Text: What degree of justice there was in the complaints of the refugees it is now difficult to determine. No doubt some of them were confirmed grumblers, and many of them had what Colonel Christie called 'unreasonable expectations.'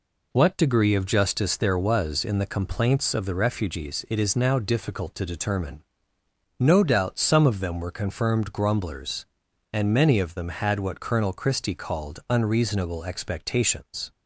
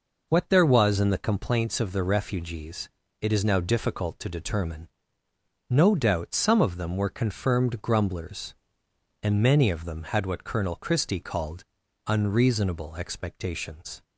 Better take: first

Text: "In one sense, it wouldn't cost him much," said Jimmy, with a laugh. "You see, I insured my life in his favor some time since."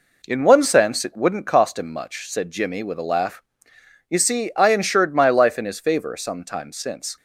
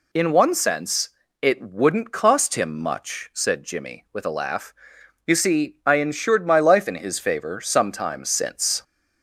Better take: neither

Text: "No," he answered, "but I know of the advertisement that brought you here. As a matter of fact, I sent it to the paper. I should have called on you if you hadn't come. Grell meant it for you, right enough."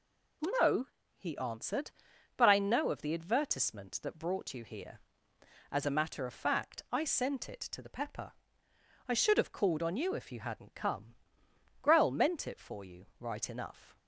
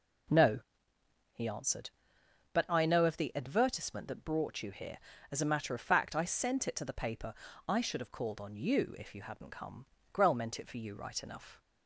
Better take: second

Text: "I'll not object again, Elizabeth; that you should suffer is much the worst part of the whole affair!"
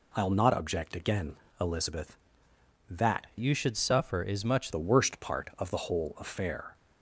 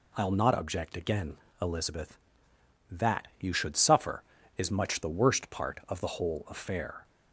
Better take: second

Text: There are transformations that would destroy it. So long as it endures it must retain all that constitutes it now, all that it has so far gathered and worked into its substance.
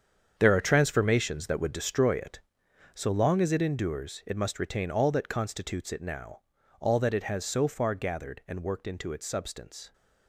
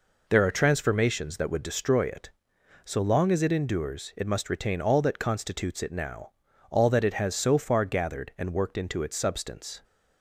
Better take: second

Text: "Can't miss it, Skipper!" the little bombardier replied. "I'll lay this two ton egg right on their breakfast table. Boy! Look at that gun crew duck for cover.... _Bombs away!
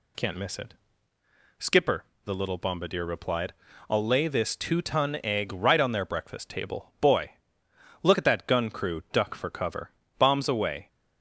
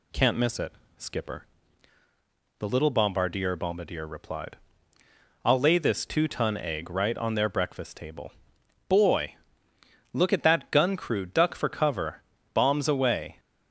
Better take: first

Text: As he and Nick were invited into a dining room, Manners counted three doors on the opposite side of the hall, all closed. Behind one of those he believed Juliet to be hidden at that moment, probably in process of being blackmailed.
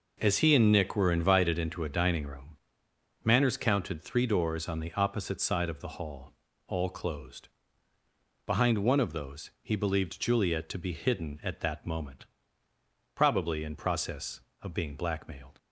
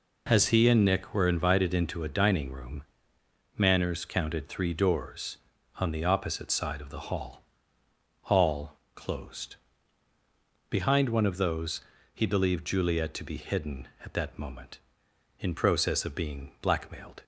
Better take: first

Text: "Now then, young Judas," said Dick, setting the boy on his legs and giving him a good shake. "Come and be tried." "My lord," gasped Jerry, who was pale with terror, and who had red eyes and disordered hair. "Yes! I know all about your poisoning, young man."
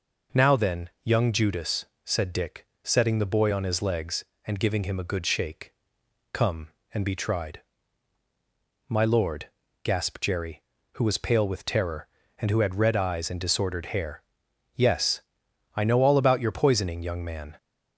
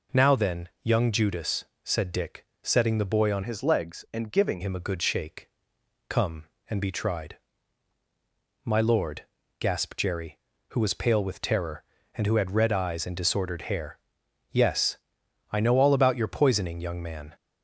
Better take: first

